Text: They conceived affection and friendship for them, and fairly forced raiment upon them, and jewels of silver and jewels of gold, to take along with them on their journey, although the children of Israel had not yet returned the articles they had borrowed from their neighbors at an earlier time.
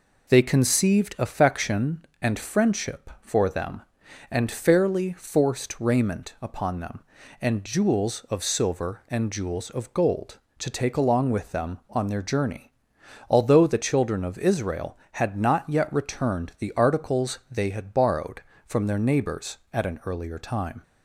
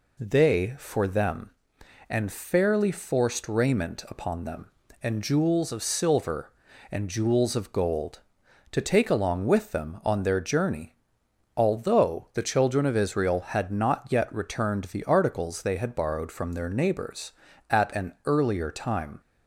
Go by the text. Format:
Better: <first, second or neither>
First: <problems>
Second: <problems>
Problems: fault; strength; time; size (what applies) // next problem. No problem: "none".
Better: first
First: none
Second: skips "conceived affection and friendship"; at 0.7 s